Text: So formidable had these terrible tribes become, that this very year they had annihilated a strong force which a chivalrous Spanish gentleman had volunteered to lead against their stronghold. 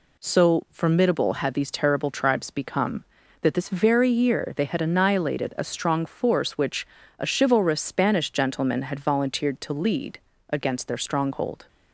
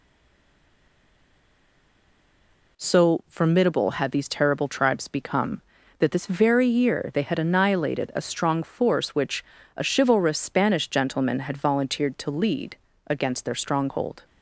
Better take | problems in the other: first | stays silent before the first word; strong; until 2.7 s; 2.7 s long // pauses between "which" and "a"; slight; at 9.4 s; 0.32 s long; slight in the first // pauses between "lead" and "against"; slight; at 12.7 s; 0.30 s long; slight in the first

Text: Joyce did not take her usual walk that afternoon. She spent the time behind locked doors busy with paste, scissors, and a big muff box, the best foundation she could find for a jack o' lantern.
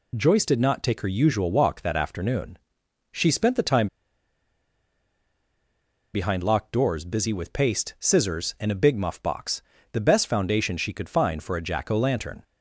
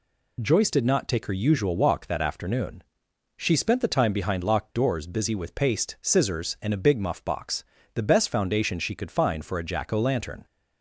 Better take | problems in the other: second | pauses between "time" and "behind"; strong; at 3.8 s; 2.2 s long

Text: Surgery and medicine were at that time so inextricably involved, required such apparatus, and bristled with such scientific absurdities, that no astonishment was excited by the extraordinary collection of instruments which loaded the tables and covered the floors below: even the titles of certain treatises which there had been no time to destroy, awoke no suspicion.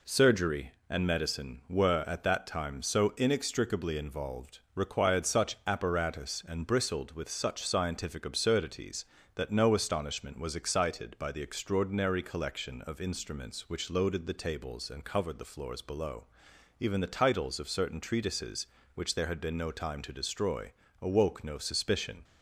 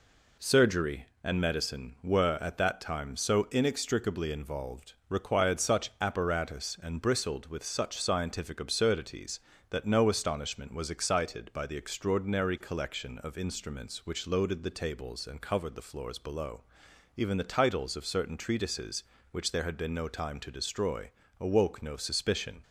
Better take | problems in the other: neither | none

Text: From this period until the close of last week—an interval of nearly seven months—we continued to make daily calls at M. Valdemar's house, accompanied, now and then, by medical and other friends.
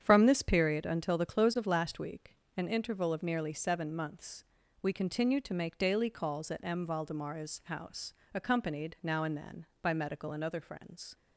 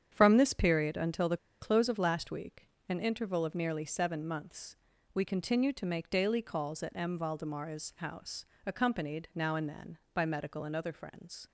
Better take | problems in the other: first | starts louder than the rest; strong; until 1.1 s; 8.5 dB; strong in the first // pauses between "the" and "close"; slight; at 1.3 s; 0.23 s long

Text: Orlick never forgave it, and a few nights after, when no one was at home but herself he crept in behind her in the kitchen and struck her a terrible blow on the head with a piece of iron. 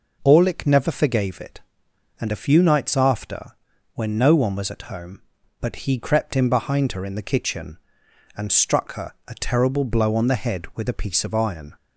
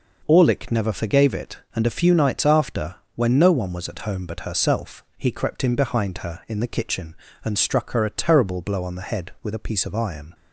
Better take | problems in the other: second | skips "herself"; at 5.7 s // pauses between "her" and "a"; slight; at 9.1 s; 0.16 s long

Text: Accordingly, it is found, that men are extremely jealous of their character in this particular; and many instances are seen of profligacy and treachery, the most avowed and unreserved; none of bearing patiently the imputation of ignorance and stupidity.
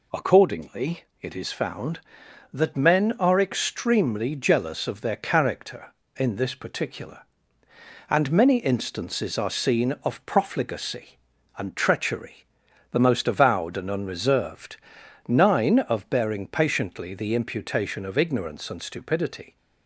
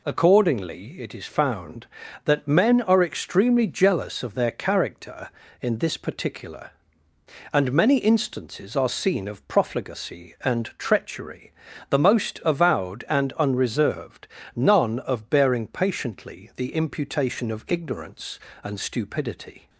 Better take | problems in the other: second | says "nine" for "none"; at 15.2 s

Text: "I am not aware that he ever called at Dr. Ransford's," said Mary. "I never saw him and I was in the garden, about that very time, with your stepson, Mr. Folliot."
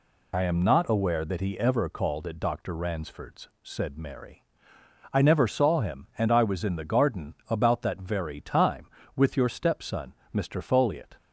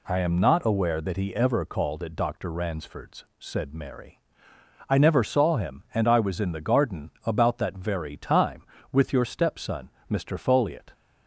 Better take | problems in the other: second | loses the start of "I"; at 0.3 s; 45 ms

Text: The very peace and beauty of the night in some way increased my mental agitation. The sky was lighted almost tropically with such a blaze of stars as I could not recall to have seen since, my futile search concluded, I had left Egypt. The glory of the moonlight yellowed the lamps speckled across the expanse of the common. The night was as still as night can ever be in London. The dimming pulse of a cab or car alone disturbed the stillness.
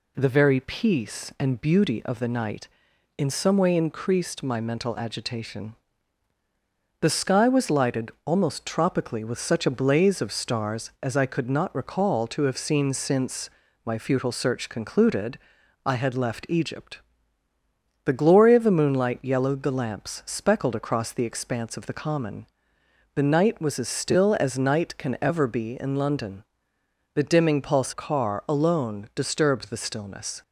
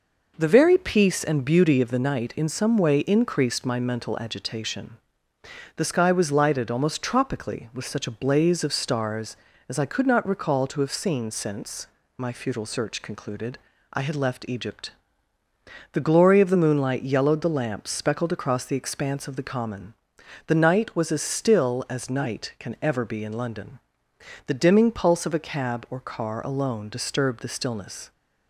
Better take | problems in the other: second | skips "of a cab or"; at 27.9 s

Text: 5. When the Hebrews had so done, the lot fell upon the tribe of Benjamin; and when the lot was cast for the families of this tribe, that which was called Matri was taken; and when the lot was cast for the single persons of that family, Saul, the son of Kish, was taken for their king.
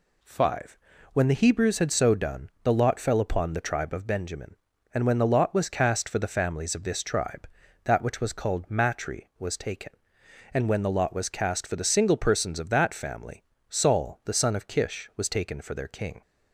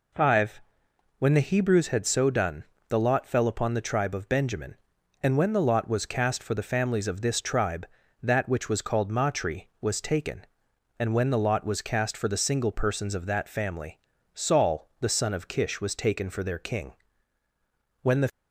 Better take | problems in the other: first | goes on to say "When the"; slight; from 18.0 s on; 0.26 s long

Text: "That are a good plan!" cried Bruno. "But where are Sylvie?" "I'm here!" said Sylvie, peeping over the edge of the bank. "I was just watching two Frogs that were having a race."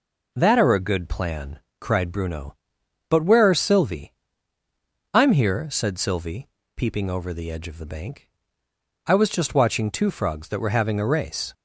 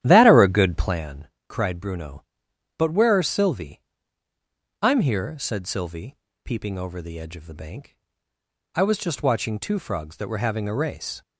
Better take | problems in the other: first | starts louder than the rest; strong; until 1.0 s; 11.5 dB

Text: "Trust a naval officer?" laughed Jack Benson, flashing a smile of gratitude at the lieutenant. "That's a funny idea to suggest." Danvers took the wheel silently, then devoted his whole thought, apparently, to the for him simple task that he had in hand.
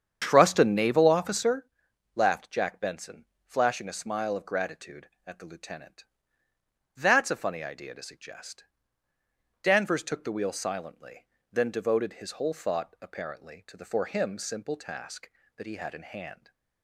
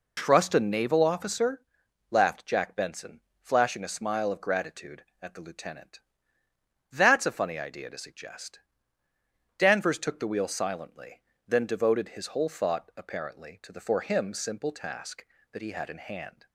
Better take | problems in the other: second | starts louder than the rest; strong; until 1.6 s; 8 dB

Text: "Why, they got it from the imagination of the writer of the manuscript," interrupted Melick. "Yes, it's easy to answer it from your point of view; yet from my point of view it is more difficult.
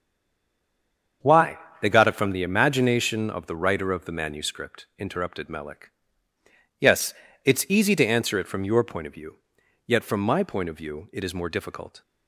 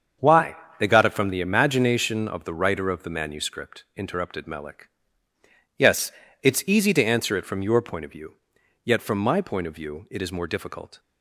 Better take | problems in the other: second | stays silent before the first word; noticeable; until 1.2 s; 1.2 s long // starts louder than the rest; until 2.4 s; 7 dB; also in the second

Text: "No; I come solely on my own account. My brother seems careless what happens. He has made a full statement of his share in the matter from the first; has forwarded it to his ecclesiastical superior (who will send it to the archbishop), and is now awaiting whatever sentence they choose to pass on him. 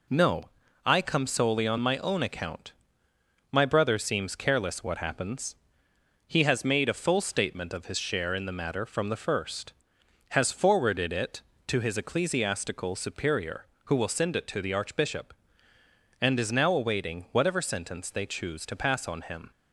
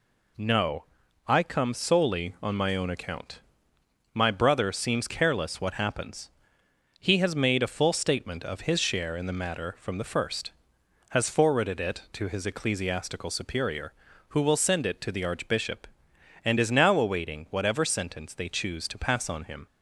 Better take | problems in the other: neither | none

